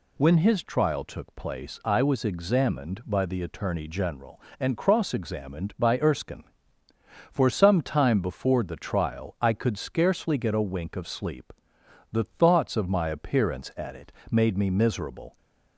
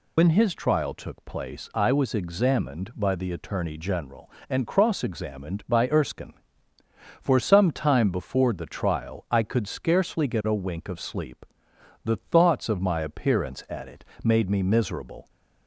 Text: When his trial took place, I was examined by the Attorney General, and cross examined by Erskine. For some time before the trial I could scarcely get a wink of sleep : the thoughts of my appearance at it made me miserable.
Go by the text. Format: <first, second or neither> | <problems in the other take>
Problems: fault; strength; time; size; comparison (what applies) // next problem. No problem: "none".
first | loses the start of "When"; at 0.1 s; 75 ms // pauses between "it" and "made"; slight; at 14.0 s; 0.18 s long; slight in the first